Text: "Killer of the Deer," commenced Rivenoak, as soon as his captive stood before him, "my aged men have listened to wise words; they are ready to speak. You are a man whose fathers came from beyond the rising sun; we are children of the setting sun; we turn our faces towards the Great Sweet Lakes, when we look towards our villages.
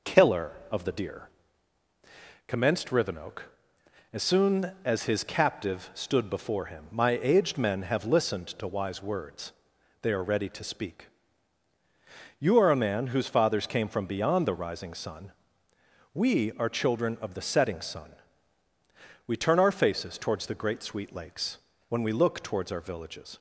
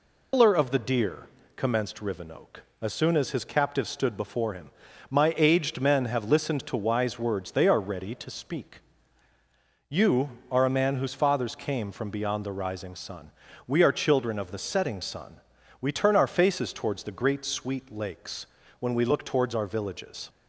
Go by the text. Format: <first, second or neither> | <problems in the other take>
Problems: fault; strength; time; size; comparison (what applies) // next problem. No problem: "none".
first | loses the start of "Killer"; at 0.3 s; 165 ms